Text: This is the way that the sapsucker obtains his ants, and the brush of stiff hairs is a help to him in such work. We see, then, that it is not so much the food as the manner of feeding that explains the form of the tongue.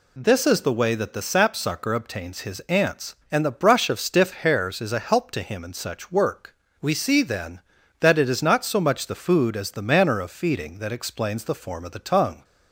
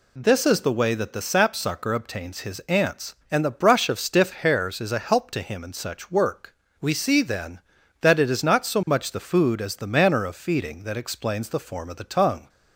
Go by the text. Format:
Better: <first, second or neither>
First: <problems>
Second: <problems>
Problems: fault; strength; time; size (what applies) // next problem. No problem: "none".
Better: neither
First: none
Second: none